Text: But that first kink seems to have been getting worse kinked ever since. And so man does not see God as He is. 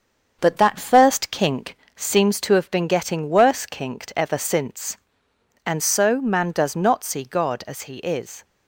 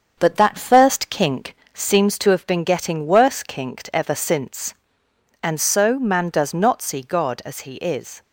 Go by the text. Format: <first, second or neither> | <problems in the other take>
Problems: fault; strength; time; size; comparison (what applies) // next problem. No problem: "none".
neither | starts louder than the rest; the same in both // pauses between "kink" and "seems"; slight; the same in both